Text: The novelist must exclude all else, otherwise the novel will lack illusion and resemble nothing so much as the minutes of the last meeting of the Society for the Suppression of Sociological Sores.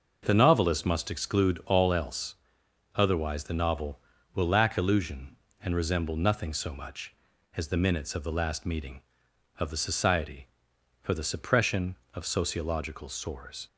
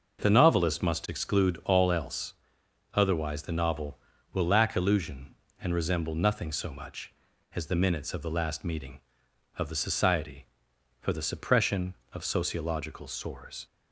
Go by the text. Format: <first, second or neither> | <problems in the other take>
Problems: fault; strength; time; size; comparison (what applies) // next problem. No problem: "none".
neither | none